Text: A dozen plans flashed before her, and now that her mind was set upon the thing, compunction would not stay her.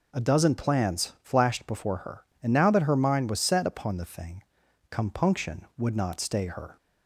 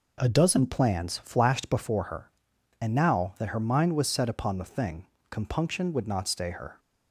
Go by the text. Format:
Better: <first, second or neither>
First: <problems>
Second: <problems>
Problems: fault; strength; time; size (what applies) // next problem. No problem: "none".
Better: neither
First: none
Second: none